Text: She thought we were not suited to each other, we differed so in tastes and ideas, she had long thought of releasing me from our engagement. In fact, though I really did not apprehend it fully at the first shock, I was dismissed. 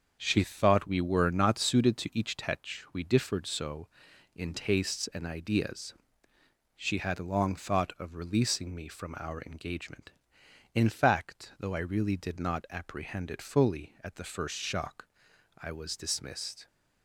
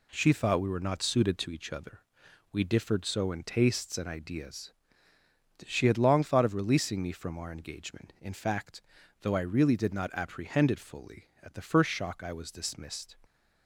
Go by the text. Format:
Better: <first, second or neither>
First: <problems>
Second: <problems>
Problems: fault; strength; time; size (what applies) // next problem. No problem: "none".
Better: second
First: starts louder than the rest; until 1.2 s; 6.5 dB // says "tetch" for "other"; at 2.3 s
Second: none